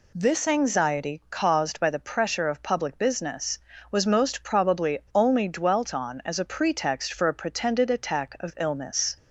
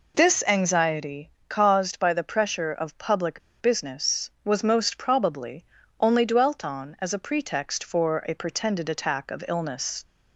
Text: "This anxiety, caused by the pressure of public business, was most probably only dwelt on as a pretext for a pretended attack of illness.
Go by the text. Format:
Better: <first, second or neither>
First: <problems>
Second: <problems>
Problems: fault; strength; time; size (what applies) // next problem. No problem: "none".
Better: first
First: none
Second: pauses between "public" and "business"; slight; at 3.4 s; 0.21 s long // pauses between "probably" and "only"; slight; at 5.6 s; 0.36 s long